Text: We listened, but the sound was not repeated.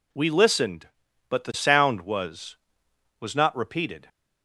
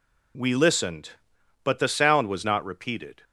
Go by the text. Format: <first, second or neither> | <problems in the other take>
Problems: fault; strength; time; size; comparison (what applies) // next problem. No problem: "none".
second | says "was" twice; at 3.2 s